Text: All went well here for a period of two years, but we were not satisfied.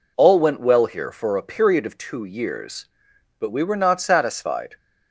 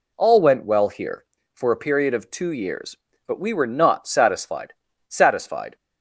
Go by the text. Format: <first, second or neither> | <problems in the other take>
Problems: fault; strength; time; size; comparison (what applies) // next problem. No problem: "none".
first | says "satisfied" twice; at 5.0 s